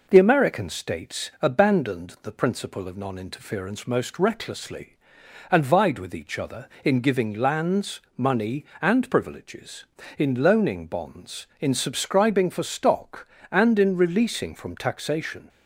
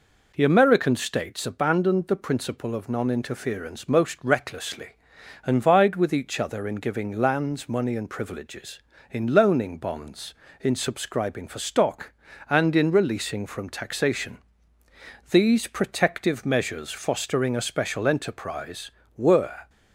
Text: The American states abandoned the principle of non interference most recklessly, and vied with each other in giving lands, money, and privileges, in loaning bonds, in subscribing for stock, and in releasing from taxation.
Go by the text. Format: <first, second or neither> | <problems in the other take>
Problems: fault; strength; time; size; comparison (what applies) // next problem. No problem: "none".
first | goes on to say "These protective measures fostering a special enterprise were"; strong; from 15.3 s on; 4.3 s long